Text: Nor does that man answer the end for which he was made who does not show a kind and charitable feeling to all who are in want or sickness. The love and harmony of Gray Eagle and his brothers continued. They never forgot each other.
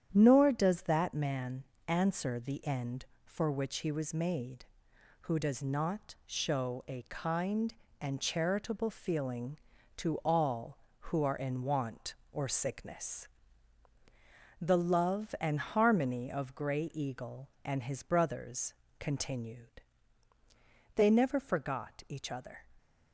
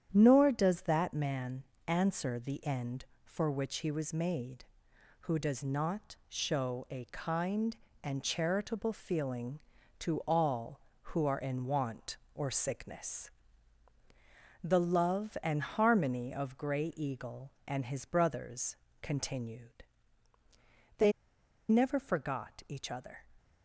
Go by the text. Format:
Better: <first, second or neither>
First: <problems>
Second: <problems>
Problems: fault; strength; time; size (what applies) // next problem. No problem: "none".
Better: first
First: starts louder than the rest; strong; until 1.1 s; 9 dB // pauses between "man" and "answer"; slight; at 1.6 s; 0.24 s long // pauses between "brothers" and "continued"; slight; at 18.7 s; 0.24 s long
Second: starts louder than the rest; strong; until 1.1 s; 9 dB // pauses between "man" and "answer"; slight; at 1.6 s; 0.24 s long // pauses between "brothers" and "continued"; slight; at 18.7 s; 0.24 s long // pauses between "They" and "never"; noticeable; at 21.1 s; 0.57 s long